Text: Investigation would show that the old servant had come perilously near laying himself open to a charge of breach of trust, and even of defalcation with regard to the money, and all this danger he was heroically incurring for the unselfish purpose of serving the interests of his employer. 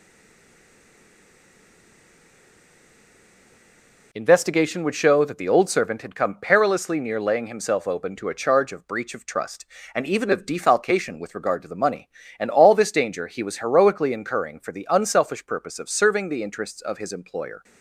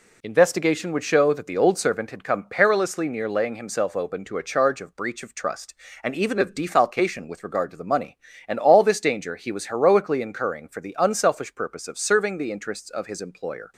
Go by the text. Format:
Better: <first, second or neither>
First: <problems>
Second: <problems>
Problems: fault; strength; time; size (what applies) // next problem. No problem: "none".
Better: second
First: stays silent before the first word; strong; until 4.1 s; 4.1 s long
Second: none